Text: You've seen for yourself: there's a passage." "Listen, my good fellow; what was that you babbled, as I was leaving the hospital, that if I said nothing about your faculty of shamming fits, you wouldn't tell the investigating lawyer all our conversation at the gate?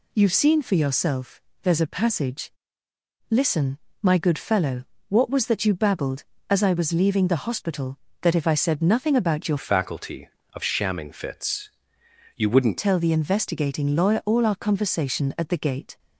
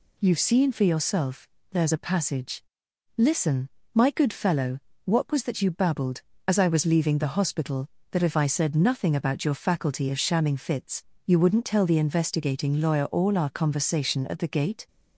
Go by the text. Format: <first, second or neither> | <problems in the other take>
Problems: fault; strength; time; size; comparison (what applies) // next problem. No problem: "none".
second | changes voice from "faculty" to "wouldn't"; from 9.5 to 12.7 s; 3.2 s long